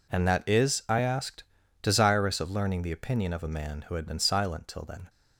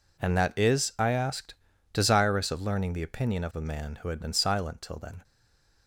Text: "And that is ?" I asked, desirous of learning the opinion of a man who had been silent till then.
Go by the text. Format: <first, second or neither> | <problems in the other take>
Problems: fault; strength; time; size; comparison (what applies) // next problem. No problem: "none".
first | stays silent after the last word; slight; from 5.2 s on; 0.6 s long